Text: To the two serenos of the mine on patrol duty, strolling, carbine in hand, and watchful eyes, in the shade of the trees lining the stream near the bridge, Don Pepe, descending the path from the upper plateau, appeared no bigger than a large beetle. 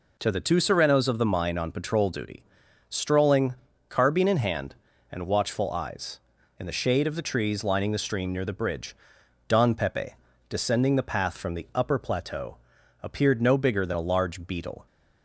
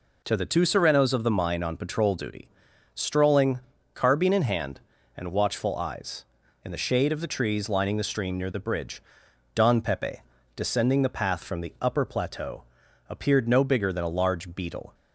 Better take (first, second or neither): neither